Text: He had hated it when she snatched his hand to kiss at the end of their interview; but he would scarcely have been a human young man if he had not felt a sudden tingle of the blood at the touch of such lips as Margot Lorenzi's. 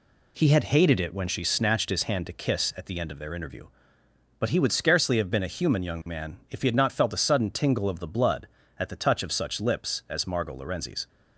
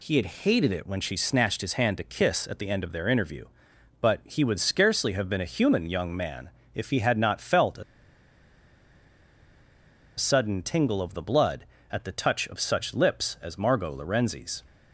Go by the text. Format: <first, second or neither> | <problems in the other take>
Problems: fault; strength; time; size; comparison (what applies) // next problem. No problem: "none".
first | pauses between "man" and "if"; slight; at 6.5 s; 0.24 s long // pauses between "a" and "sudden"; strong; at 7.8 s; 2.3 s long